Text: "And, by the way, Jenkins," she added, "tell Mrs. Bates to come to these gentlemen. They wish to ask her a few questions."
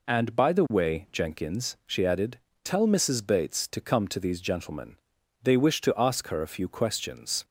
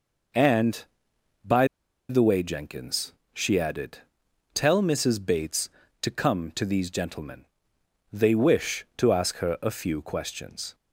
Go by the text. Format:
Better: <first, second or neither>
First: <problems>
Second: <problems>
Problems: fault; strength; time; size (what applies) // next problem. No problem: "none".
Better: first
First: none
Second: pauses between "by" and "the"; at 1.6 s; 0.42 s long